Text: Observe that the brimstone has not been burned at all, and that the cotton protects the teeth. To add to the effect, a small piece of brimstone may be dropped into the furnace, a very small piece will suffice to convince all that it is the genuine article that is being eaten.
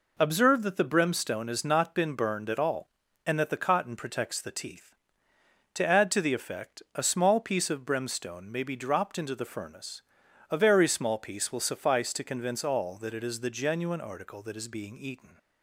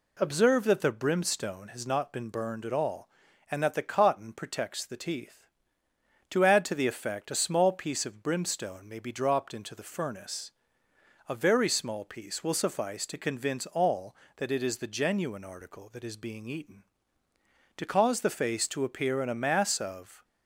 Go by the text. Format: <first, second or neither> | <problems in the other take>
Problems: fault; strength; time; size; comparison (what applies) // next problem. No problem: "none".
first | goes on to say "To cause the face to appear in a mass of"; strong; from 17.7 s on; 2.4 s long